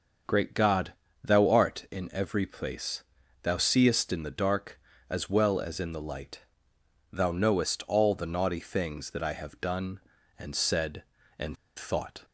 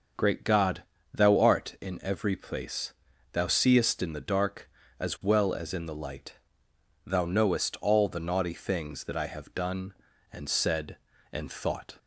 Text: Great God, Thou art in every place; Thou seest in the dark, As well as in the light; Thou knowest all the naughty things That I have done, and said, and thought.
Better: second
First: starts louder than the rest; noticeable; until 1.5 s; 6 dB // pauses between "and" and "thought"; slight; at 11.5 s; 0.22 s long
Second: starts louder than the rest; until 1.4 s; 6.5 dB

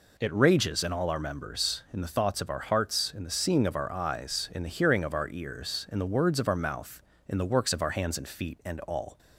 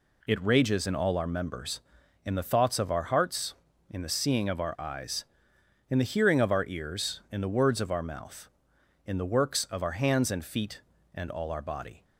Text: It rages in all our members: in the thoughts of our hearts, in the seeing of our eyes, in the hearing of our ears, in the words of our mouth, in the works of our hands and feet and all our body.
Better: second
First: stops before "our body"; at 9.1 s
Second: none

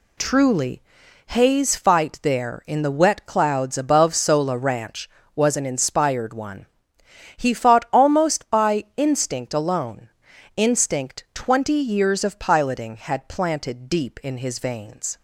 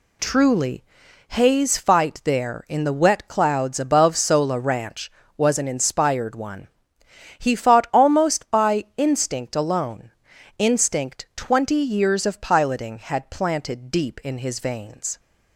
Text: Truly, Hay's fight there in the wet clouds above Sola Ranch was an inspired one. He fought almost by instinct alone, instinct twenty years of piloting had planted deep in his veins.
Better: neither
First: none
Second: none

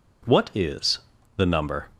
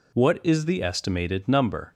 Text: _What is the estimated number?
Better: second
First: pauses between "is" and "the"; slight; at 0.9 s; 0.36 s long // skips "estimated"; at 1.4 s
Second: none

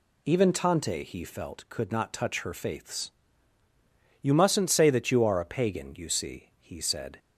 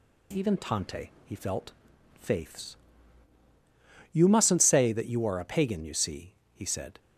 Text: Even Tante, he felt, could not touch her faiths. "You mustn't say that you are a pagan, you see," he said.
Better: first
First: none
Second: skips "could not touch her"; at 1.9 s

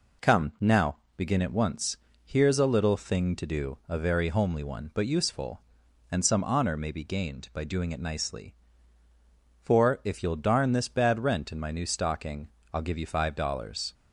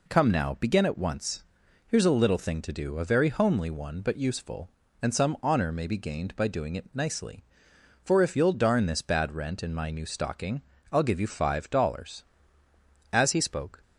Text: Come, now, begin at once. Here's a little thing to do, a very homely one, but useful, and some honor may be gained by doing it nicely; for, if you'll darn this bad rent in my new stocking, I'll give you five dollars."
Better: first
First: none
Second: goes on to say "As he spoke"; noticeable; from 13.1 s on; 0.70 s long

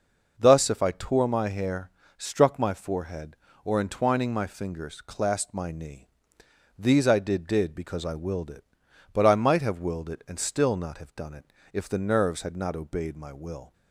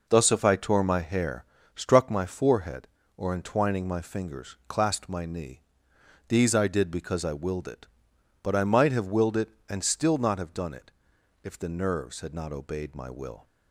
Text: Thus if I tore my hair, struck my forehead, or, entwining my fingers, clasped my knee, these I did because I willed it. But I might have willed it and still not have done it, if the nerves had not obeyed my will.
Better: second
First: says "did" twice; at 7.4 s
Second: none

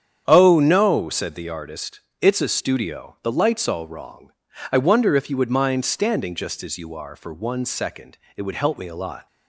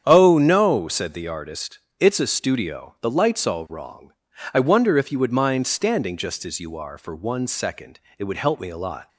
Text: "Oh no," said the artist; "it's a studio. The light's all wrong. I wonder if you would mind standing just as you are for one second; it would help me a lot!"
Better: neither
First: starts louder than the rest; strong; until 1.2 s; 8.5 dB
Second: starts louder than the rest; strong; until 1.0 s; 8.5 dB

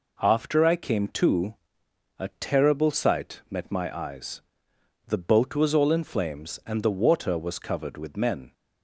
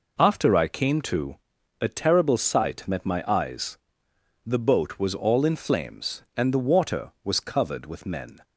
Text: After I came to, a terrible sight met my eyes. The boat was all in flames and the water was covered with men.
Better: neither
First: none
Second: none

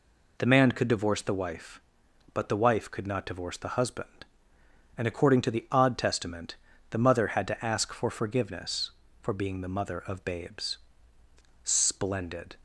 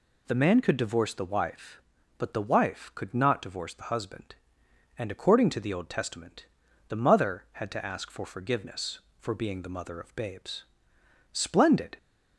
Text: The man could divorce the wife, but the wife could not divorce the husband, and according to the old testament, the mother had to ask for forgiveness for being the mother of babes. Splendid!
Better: second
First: says "odd" for "old"; at 5.7 s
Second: none

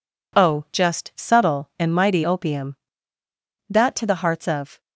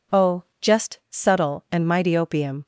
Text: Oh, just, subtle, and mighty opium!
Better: second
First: goes on to say "that to the hearts of"; noticeable; from 3.6 s on; 1.1 s long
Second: none

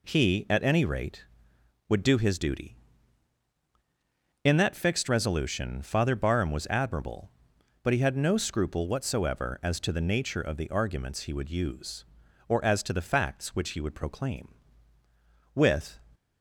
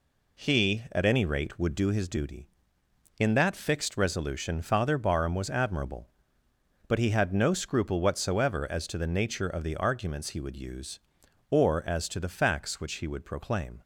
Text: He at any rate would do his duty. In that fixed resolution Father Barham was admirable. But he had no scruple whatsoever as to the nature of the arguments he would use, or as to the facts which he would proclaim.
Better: second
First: goes on to say "With"; slight; from 15.5 s on; 0.42 s long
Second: none

